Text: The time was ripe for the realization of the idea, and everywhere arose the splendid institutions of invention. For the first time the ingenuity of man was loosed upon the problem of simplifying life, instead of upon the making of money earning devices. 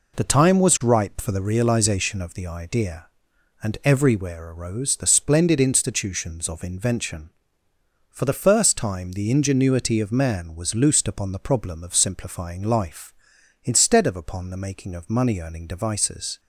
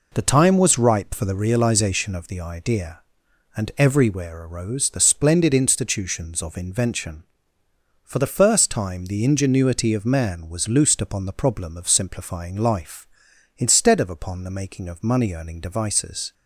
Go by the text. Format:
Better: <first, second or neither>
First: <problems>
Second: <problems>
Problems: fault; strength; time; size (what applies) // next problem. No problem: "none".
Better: neither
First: none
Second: none